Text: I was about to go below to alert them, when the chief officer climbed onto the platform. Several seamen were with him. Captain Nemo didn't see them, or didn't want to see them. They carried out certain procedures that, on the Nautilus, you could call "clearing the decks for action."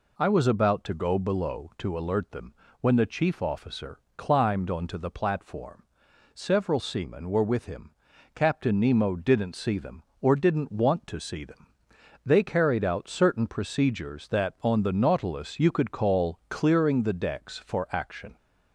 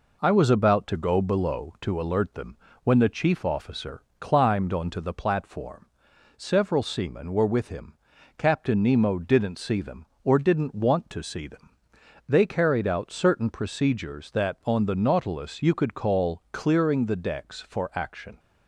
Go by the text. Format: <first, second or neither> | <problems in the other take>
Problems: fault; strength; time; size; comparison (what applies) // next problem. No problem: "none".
first | gets quieter; slight; throughout; 2.5 dB // pauses between "officer" and "climbed"; slight; at 4.0 s; 0.16 s long; slight in the first